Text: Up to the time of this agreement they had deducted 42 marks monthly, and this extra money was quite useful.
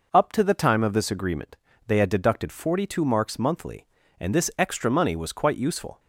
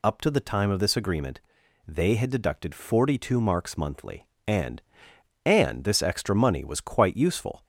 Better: first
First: pauses between "agreement" and "they"; slight; at 1.5 s; 0.30 s long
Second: pauses between "agreement" and "they"; noticeable; at 1.3 s; 0.48 s long // says "and" twice; at 5.4 s

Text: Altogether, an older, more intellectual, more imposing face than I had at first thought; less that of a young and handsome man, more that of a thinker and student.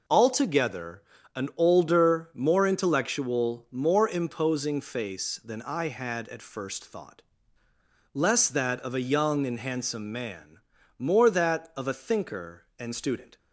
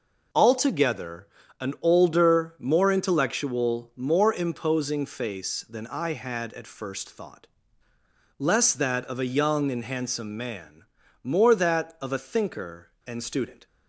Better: neither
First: none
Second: none

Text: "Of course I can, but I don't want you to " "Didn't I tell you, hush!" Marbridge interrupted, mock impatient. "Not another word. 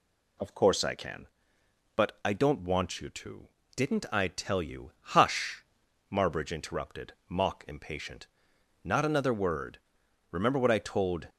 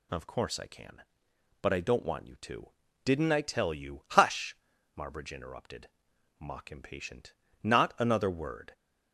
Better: second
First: goes on to say "Remember what I told"; noticeable; from 10.2 s on; 1.0 s long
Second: none

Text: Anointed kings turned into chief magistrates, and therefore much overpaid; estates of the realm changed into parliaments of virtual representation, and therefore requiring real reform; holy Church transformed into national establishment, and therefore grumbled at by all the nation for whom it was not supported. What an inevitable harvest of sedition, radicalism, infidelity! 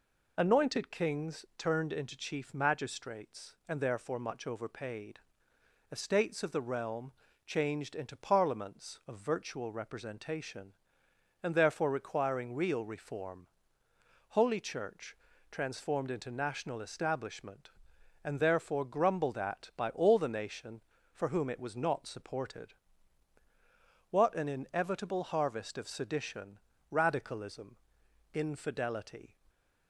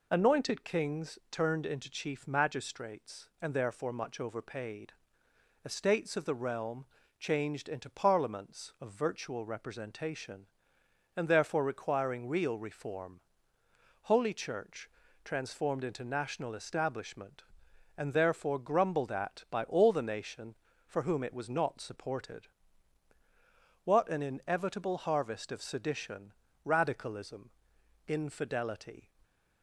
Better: neither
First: pauses between "realm" and "changed"; slight; at 7.1 s; 0.34 s long // pauses between "Church" and "transformed"; slight; at 15.1 s; 0.32 s long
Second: pauses between "realm" and "changed"; slight; at 6.8 s; 0.34 s long // pauses between "Church" and "transformed"; slight; at 14.9 s; 0.32 s long

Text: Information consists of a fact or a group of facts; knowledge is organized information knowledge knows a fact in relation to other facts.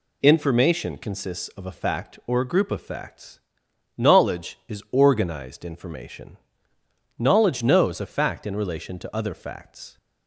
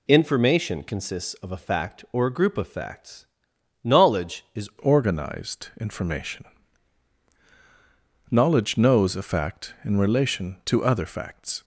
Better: first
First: pauses between "information" and "knowledge"; noticeable; at 6.3 s; 0.80 s long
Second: changes voice at "organized"; from 4.8 s on; 6.8 s long // pauses between "information" and "knowledge"; strong; at 6.4 s; 1.8 s long

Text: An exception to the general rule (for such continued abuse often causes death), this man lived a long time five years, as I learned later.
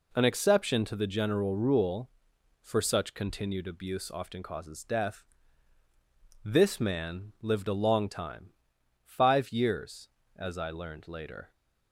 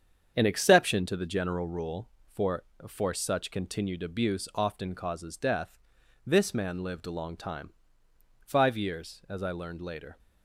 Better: first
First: pauses between "time" and "five"; noticeable; at 8.5 s; 0.56 s long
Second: starts louder than the rest; strong; until 1.3 s; 7.5 dB // says "for" twice; at 2.8 s // pauses between "time" and "five"; noticeable; at 7.7 s; 0.74 s long

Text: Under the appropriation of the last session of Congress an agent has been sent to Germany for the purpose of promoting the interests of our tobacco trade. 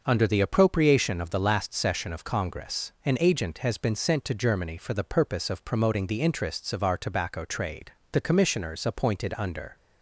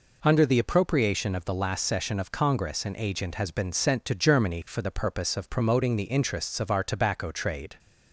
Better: second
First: goes on to say "The commissioners appointed under"; from 8.1 s on; 1.6 s long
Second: none

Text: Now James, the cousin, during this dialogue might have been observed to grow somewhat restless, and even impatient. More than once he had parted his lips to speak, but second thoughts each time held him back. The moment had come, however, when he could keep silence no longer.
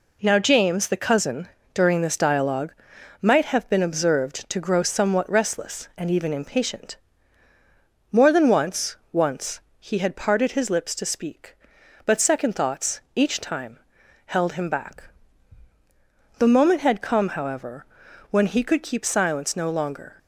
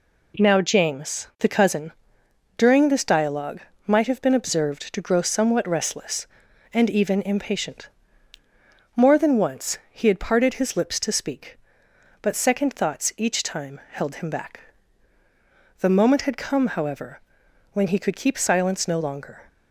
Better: second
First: pauses between "dialogue" and "might"; noticeable; at 2.7 s; 0.48 s long // says "once" twice; at 9.1 s // pauses between "time" and "held"; noticeable; at 13.7 s; 0.48 s long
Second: pauses between "dialogue" and "might"; slight; at 3.6 s; 0.26 s long

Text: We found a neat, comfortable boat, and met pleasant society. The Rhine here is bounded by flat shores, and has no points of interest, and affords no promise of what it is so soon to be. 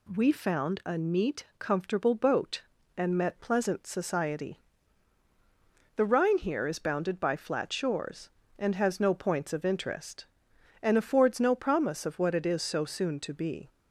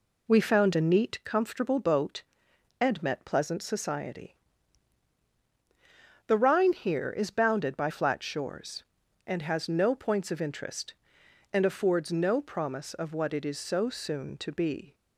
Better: first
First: none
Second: starts louder than the rest; slight; until 1.4 s; 2.5 dB

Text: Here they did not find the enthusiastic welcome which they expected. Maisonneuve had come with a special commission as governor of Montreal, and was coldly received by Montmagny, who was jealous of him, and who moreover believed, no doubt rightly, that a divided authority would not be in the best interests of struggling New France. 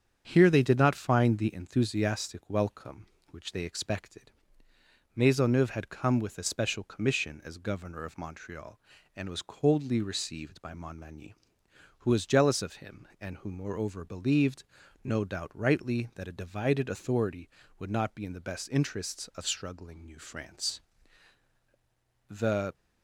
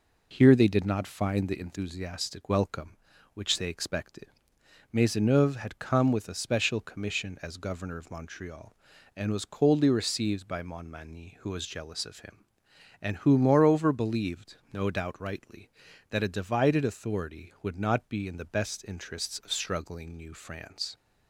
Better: second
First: starts louder than the rest; strong; until 1.2 s; 7.5 dB // goes on to say "The"; slight; from 22.2 s on; 0.44 s long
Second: none

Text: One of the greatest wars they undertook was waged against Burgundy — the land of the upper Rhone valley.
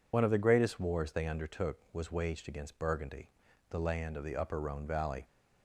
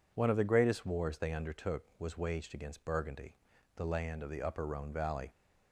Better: second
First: loses the start of "One"; at 0.1 s; 50 ms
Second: none

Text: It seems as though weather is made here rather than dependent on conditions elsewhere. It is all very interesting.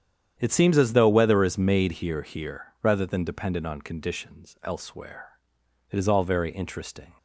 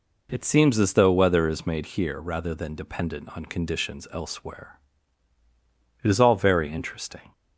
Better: second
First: starts louder than the rest; strong; until 1.3 s; 9.5 dB // says "here" twice; at 2.2 s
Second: none

